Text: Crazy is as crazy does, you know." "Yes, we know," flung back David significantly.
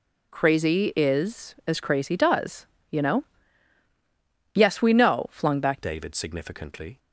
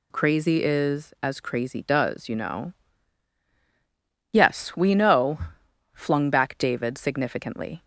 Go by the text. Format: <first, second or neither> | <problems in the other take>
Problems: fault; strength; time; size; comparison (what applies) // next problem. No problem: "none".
second | changes voice at "David"; from 5.8 s on; 1.1 s long